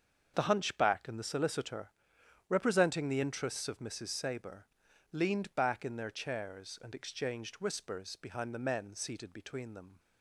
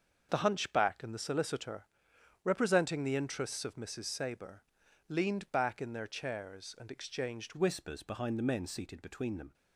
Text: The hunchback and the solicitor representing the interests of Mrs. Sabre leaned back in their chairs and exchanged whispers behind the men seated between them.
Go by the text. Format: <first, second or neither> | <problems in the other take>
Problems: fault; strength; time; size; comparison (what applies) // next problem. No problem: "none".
first | starts louder than the rest; until 1.3 s; 6.5 dB; also in the first // pauses between "solicitor" and "representing"; noticeable; at 1.8 s; 0.58 s long; noticeable in the first // pauses between "Sabre" and "leaned"; noticeable; at 4.6 s; 0.46 s long; noticeable in the first // changes voice at "whispers"; from 7.5 s on; 2.0 s long